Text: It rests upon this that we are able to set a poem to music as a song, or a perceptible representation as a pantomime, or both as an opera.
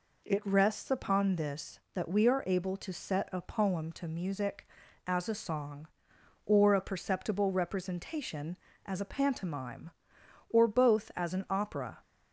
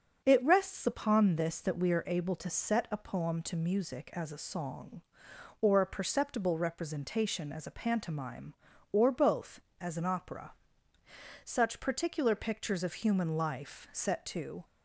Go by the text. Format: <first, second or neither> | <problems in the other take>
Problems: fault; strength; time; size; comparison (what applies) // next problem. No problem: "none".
first | starts louder than the rest; until 1.2 s; 6.5 dB // goes on to say "Such particular pictures of human life set to"; strong; from 11.4 s on; 3.2 s long